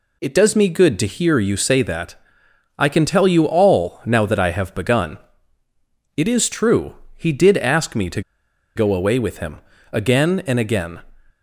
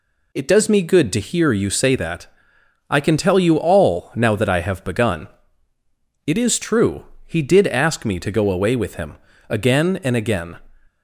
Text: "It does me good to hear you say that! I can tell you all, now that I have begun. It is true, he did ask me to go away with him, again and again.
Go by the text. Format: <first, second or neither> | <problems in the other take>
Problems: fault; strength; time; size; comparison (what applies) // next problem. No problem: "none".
second | pauses between "to" and "go"; noticeable; at 8.2 s; 0.55 s long